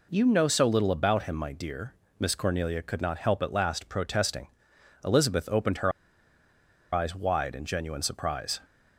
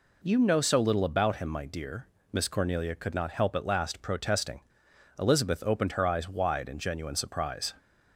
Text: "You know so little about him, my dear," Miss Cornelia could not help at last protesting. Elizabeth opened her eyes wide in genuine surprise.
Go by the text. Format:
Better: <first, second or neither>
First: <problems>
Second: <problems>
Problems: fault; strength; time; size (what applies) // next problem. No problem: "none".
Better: second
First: pauses between "her" and "eyes"; at 5.9 s; 1.0 s long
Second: none